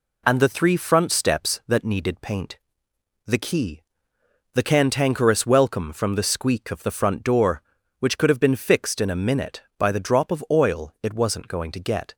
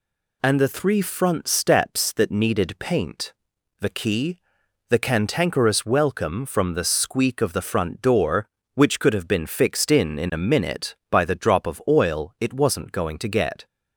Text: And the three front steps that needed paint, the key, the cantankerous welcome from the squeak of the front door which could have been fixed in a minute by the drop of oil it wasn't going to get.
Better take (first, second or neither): first